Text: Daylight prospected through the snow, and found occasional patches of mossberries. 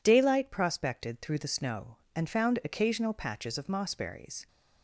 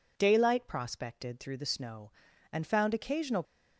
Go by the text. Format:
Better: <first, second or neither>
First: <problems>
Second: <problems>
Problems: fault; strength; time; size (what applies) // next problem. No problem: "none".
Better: first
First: none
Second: stops before "patches of mossberries"; at 3.4 s